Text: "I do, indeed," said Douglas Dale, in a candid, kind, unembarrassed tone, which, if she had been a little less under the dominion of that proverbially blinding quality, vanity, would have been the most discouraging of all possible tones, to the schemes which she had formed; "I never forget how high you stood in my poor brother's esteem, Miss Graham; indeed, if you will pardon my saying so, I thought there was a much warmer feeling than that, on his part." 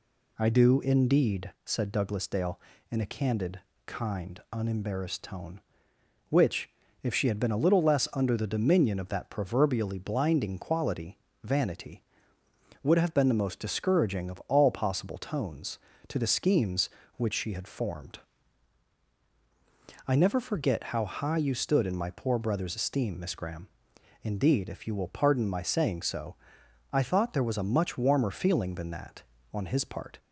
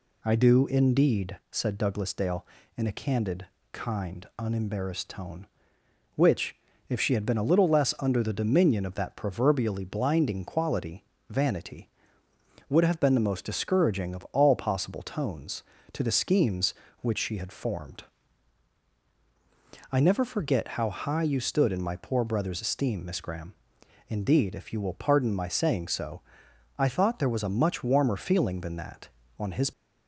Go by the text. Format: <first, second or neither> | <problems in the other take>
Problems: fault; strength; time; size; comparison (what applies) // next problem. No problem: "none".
first | stops before "part"; at 29.7 s